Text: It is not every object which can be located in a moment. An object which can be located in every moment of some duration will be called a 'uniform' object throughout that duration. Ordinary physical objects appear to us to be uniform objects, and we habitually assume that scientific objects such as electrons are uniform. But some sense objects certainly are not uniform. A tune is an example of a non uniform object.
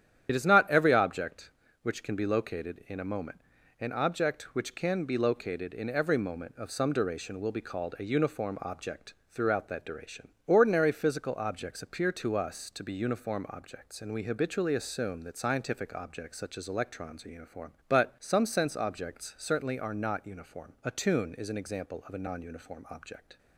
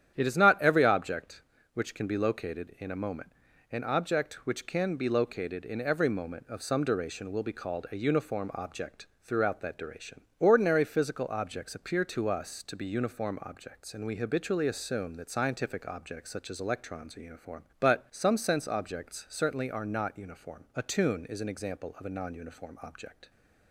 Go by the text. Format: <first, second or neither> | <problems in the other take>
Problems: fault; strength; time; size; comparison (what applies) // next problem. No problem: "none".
second | loses the start of "It"; at 0.2 s; 55 ms // starts louder than the rest; strong; until 1.3 s; 10 dB; strong in the second // pauses between "object" and "throughout"; slight; at 9.1 s; 0.16 s long; slight in the second